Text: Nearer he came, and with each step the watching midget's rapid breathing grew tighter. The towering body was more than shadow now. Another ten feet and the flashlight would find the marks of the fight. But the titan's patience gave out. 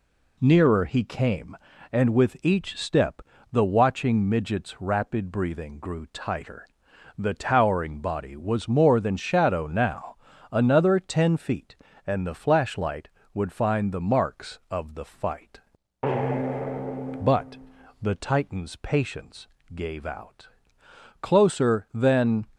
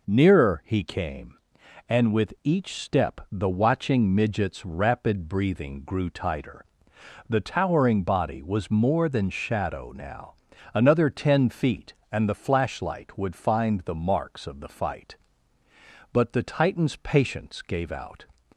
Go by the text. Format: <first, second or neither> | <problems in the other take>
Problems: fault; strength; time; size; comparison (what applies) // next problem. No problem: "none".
second | pauses between "step" and "the"; slight; at 3.2 s; 0.30 s long // pauses between "But" and "the"; at 17.5 s; 0.44 s long // pauses between "patience" and "gave"; slight; at 19.4 s; 0.32 s long // goes on to say "Closer than"; noticeable; from 21.2 s on; 1.2 s long